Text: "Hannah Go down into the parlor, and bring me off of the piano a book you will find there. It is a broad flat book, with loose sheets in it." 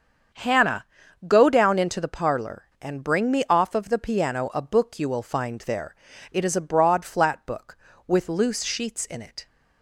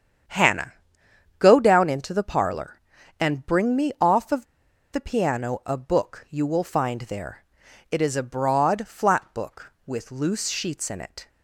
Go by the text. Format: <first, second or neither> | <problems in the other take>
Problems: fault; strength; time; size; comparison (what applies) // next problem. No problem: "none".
first | starts louder than the rest; strong; until 1.9 s; 8.5 dB; strong in the first // pauses between "Hannah" and "Go"; noticeable; at 0.7 s; 0.66 s long; also in the first // pauses between "of" and "the"; noticeable; at 4.4 s; 0.48 s long